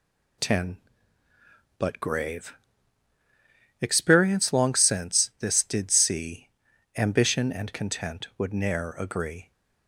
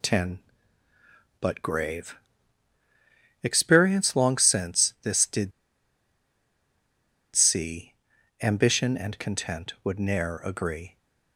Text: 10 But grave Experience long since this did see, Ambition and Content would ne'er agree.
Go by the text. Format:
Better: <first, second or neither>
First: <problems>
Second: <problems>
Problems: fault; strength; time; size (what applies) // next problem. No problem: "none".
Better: first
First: pauses between "grave" and "Experience"; strong; at 2.5 s; 1.2 s long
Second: pauses between "grave" and "Experience"; strong; at 2.1 s; 1.2 s long // pauses between "did" and "see"; strong; at 5.5 s; 1.8 s long